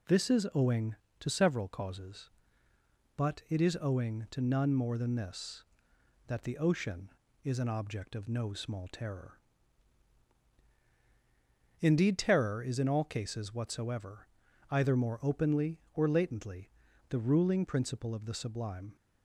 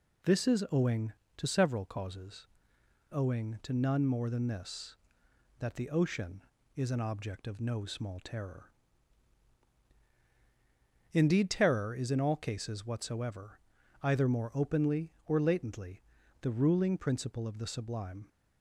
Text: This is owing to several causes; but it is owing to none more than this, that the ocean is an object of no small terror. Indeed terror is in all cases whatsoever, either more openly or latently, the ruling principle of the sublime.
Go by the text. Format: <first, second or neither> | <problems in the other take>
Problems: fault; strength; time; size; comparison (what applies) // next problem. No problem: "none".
first | skips "but it is"; at 2.7 s